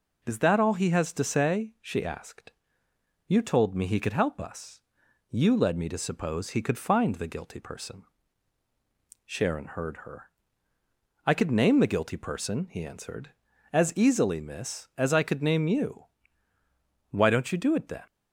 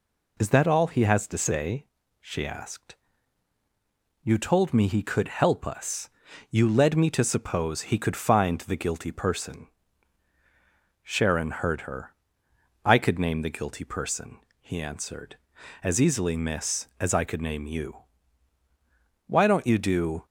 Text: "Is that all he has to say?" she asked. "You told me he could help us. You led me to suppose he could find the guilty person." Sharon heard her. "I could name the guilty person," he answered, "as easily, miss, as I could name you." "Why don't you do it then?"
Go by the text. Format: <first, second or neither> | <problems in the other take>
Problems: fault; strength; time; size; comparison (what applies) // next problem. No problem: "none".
first | stops before "it then"; at 20.2 s